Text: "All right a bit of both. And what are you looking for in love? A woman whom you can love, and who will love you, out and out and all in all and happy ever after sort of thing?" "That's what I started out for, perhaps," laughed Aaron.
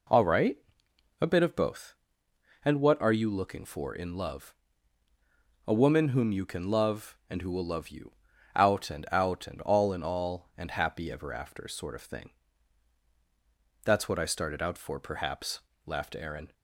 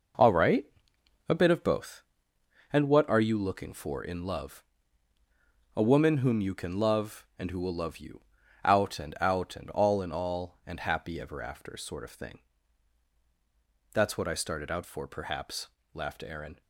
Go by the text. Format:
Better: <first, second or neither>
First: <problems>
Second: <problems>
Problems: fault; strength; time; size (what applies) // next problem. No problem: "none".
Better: first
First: pauses between "right" and "a"; noticeable; at 0.5 s; 0.64 s long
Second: gets quieter; strong; throughout; 9 dB // pauses between "right" and "a"; noticeable; at 0.6 s; 0.64 s long